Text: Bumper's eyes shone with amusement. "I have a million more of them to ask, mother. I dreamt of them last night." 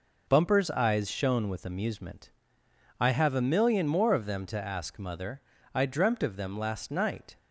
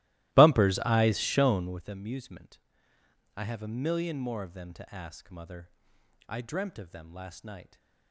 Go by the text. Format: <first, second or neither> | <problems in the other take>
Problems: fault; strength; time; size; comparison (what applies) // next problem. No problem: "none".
first | starts louder than the rest; strong; until 1.9 s; 17 dB